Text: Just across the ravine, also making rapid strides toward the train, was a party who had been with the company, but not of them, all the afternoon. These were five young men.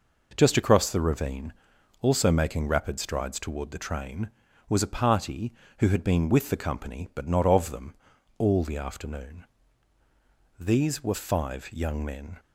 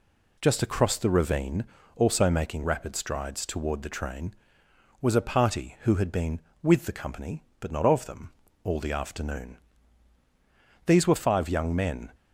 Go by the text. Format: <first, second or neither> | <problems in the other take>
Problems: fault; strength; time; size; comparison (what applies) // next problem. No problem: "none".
neither | none